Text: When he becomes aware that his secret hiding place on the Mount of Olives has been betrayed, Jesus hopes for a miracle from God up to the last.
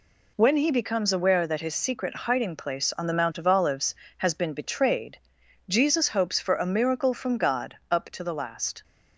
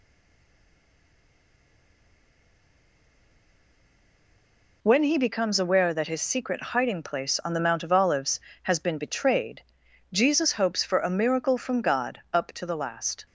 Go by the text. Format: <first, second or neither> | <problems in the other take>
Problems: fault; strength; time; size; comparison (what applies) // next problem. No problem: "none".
first | stays silent before the first word; strong; until 4.8 s; 4.8 s long